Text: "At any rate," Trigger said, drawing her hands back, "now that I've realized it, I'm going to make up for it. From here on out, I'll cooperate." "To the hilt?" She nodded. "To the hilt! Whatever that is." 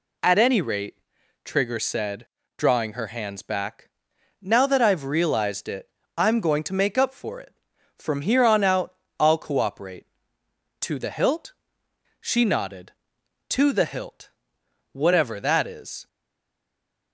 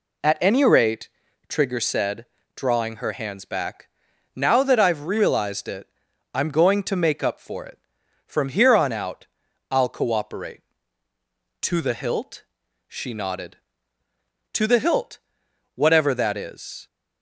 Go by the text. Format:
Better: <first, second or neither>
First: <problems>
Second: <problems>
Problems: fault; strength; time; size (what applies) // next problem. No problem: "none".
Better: second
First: stays silent after the last word; from 16.0 s on; 1.1 s long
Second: none